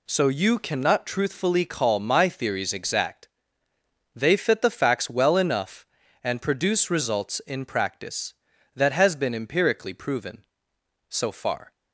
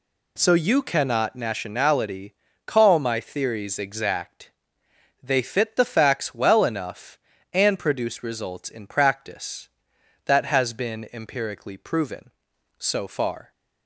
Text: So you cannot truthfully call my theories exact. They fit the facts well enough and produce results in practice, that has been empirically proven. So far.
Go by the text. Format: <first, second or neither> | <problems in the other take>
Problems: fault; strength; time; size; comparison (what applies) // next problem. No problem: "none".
first | says "nationality" for "truthfully"; at 1.3 s